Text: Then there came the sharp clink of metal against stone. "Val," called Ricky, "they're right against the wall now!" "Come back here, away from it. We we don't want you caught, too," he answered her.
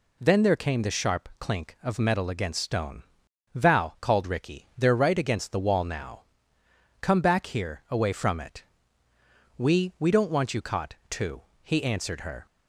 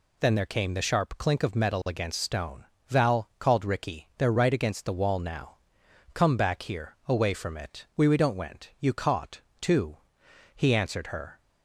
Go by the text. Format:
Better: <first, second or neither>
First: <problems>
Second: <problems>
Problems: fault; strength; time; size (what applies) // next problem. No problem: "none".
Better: first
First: none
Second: says "went" for "want"; at 8.3 s